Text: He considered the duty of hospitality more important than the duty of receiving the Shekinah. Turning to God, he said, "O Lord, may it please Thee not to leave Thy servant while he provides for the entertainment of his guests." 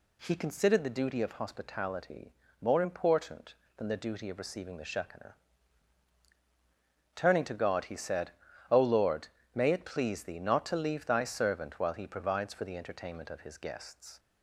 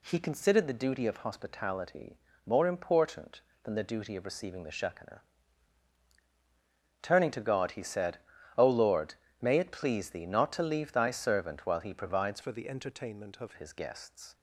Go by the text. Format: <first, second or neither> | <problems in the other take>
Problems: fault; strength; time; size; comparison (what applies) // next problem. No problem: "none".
first | pauses between "hospitality" and "more"; slight; at 2.1 s; 0.28 s long; slight in the first // changes voice from "for" to "of"; from 12.4 to 13.5 s; 1.1 s long